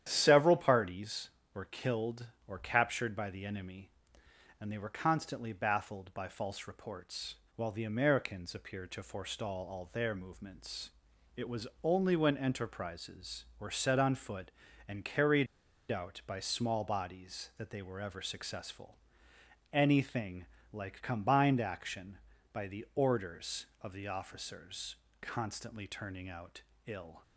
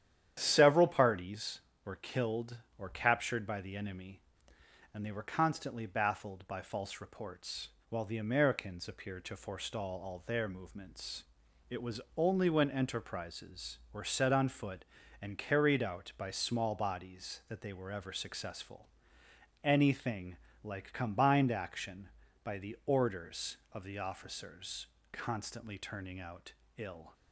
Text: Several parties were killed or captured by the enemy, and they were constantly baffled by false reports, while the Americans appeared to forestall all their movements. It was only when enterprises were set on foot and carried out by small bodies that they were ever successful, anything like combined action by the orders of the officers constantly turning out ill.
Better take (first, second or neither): second